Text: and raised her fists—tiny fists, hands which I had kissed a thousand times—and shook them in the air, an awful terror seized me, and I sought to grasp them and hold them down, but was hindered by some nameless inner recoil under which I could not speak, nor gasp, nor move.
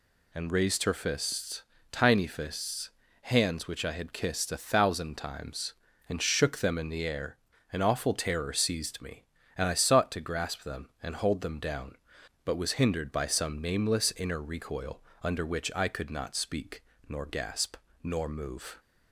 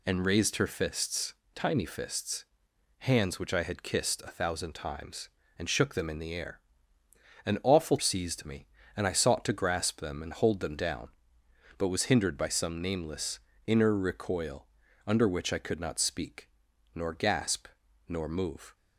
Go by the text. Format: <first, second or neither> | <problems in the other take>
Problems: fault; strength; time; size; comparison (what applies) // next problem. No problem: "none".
first | skips "terror"; at 7.9 s // pauses between "nameless" and "inner"; slight; at 13.3 s; 0.28 s long // pauses between "recoil" and "under"; at 14.6 s; 0.40 s long; slight in the first